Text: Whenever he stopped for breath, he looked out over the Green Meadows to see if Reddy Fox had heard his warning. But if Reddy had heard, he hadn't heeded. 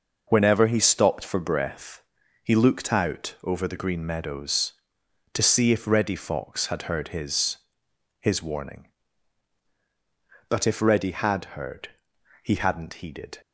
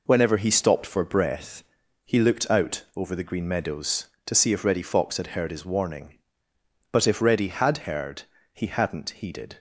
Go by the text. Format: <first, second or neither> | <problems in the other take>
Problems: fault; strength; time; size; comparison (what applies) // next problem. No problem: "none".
second | says "his" twice; at 8.2 s